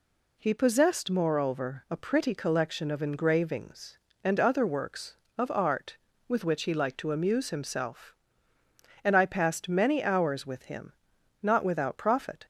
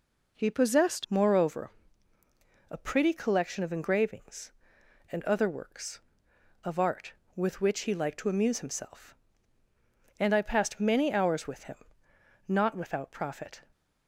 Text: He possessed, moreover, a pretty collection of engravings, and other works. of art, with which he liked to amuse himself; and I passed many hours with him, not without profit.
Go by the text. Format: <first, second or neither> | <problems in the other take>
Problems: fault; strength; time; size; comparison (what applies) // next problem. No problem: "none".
first | changes voice at "moreover"; from 1.0 s on; 12.6 s long